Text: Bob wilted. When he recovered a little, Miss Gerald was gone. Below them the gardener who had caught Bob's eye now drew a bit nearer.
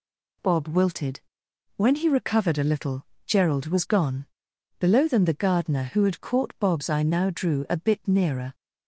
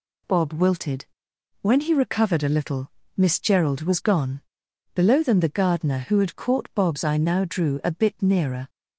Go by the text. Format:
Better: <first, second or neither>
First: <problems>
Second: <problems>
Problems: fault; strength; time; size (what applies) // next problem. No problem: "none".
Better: second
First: skips "Miss"; at 3.1 s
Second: none